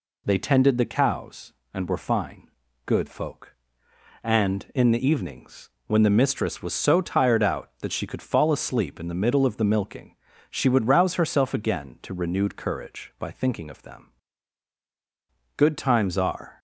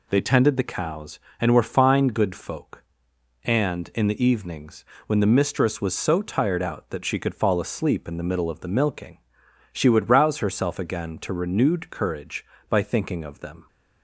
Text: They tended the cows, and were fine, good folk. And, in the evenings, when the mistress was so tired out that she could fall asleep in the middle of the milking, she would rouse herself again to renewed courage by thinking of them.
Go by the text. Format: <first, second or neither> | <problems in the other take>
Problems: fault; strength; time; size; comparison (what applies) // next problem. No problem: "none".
second | goes on to say "Good times are"; noticeable; from 15.5 s on; 1.0 s long